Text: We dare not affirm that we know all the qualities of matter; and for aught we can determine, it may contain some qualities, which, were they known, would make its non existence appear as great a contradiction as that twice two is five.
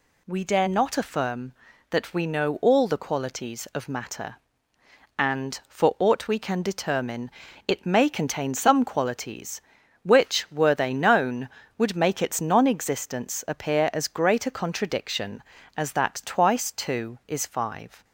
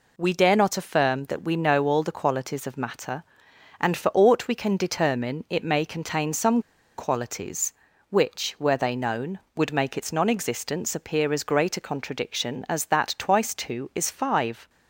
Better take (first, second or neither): first